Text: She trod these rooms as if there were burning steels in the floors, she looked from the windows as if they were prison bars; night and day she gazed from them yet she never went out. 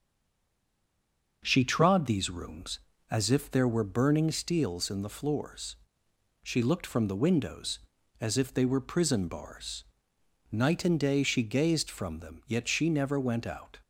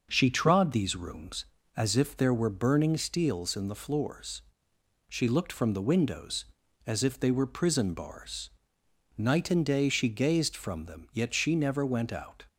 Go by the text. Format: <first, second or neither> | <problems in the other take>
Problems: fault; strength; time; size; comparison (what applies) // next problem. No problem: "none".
second | stays silent before the first word; noticeable; until 1.4 s; 1.4 s long // starts louder than the rest; until 2.4 s; 6 dB; also in the second